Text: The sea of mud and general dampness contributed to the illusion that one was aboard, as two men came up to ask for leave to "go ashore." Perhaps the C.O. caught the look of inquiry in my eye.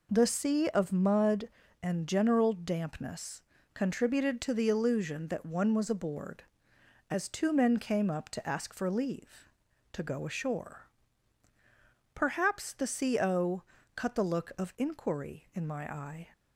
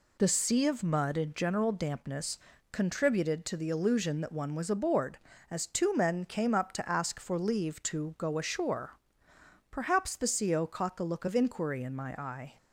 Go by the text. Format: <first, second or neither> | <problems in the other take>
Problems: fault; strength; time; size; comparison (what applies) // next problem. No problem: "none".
second | pauses between "dampness" and "contributed"; slight; at 3.4 s; 0.32 s long; slight in the second // says "cut" for "caught"; at 13.9 s